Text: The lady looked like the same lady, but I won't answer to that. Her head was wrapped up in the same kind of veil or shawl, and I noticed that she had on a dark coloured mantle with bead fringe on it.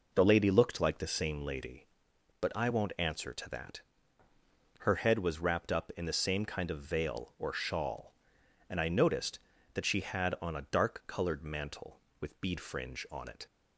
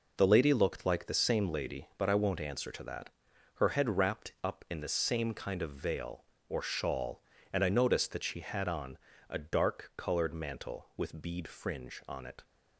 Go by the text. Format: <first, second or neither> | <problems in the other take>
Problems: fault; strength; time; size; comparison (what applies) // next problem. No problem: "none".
first | skips "was"; at 3.9 s // pauses between "on" and "a"; slight; at 8.9 s; 0.32 s long